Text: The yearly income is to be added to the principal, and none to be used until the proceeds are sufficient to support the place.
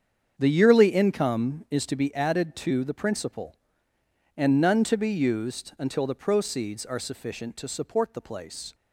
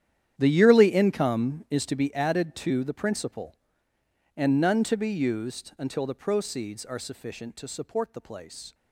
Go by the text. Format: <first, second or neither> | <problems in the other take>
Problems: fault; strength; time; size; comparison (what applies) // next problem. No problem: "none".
first | gets quieter; strong; throughout; 16 dB // starts louder than the rest; strong; until 1.3 s; 10.5 dB; strong in the first